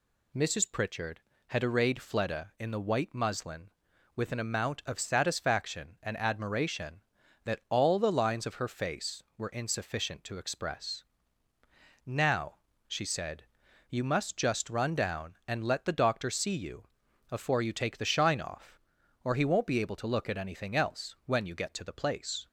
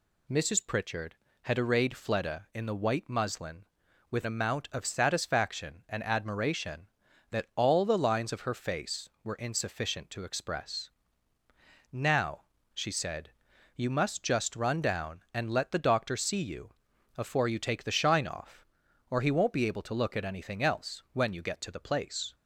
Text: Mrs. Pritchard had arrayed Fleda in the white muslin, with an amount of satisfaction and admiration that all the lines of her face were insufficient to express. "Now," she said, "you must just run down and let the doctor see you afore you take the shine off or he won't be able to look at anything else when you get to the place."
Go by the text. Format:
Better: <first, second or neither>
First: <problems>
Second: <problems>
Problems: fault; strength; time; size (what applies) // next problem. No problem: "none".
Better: first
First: pauses between "you" and "afore"; noticeable; at 16.8 s; 0.46 s long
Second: skips "an"; at 4.2 s // pauses between "you" and "afore"; noticeable; at 16.7 s; 0.46 s long